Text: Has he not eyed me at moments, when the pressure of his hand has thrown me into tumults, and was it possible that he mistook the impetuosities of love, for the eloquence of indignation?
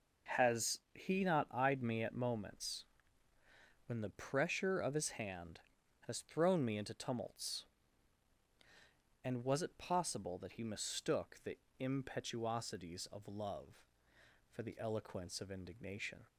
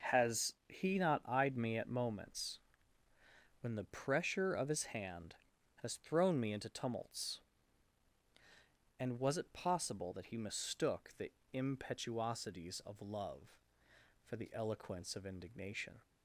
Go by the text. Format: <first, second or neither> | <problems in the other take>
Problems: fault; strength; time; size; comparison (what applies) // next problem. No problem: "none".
neither | pauses between "the" and "impetuosities"; slight; the same in both